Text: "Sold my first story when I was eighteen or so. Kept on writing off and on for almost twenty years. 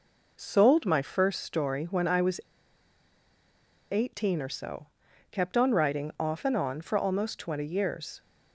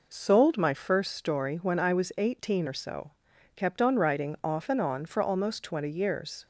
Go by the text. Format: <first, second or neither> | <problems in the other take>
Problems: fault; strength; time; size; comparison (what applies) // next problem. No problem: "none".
second | pauses between "was" and "eighteen"; strong; at 2.4 s; 1.4 s long